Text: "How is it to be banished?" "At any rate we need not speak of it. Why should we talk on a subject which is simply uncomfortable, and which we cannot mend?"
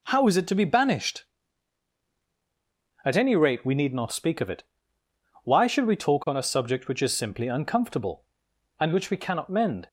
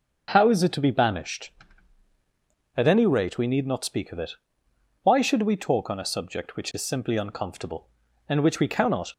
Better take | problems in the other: first | starts louder than the rest; until 1.3 s; 6.5 dB // stops before "mend"; at 9.1 s

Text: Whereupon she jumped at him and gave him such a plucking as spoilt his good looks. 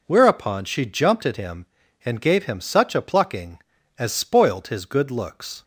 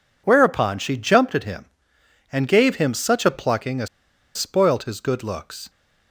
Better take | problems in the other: first | pauses between "as" and "spoilt"; noticeable; at 3.8 s; 0.49 s long

